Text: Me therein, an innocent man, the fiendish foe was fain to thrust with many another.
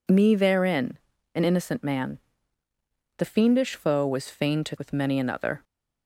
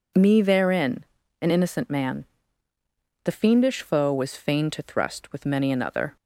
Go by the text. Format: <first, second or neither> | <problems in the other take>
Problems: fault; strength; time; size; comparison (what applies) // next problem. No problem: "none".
second | skips "thrust"; at 4.7 s